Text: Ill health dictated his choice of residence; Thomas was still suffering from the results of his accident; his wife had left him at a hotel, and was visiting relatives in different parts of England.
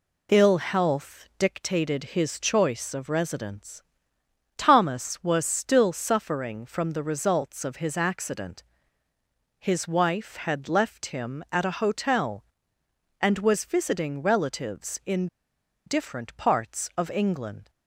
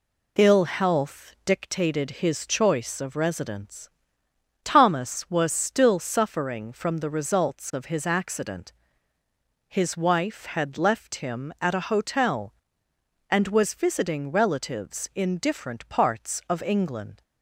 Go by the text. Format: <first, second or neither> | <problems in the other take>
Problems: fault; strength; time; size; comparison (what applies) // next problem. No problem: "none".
second | pauses between "in" and "different"; noticeable; at 15.2 s; 0.60 s long